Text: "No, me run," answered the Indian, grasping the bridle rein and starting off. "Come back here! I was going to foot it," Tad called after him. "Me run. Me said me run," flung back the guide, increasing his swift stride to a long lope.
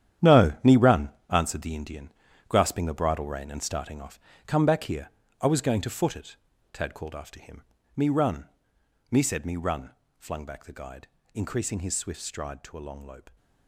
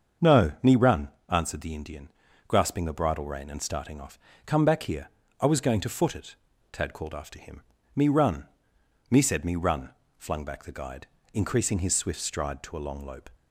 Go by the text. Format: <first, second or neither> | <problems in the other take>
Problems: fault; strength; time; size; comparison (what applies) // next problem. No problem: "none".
second | gets quieter; strong; throughout; 12 dB // starts louder than the rest; strong; until 1.5 s; 10.5 dB; also in the second